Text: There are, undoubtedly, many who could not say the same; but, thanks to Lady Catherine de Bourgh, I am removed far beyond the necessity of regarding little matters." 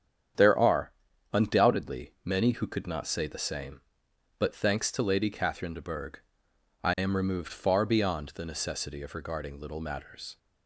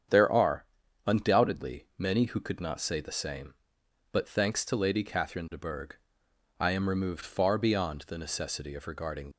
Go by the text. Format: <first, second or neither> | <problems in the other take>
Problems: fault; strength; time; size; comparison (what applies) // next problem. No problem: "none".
first | starts louder than the rest; strong; until 1.5 s; 8 dB; strong in the first // stops before "little matters"; at 9.3 s